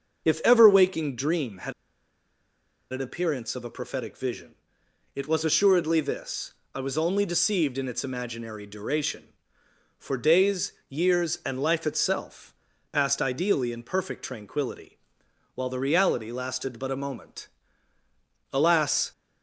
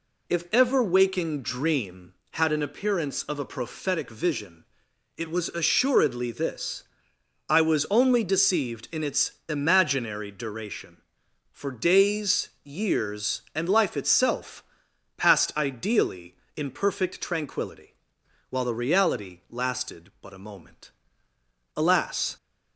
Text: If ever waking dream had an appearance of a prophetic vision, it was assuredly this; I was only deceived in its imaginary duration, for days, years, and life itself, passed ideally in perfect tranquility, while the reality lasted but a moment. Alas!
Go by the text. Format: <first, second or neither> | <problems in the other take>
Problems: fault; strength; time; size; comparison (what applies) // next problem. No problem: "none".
second | starts louder than the rest; until 1.2 s; 6.5 dB // pauses between "had" and "an"; at 1.7 s; 1.1 s long